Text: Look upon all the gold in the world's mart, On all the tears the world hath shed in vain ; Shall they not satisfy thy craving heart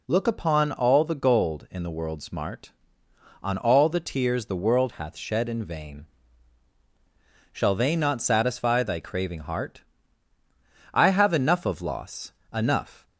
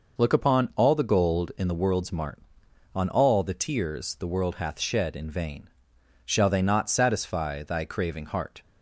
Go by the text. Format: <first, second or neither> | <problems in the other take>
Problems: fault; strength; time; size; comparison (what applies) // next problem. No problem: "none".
second | goes on to say "I have enough of loss enough"; strong; from 10.9 s on; 2.1 s long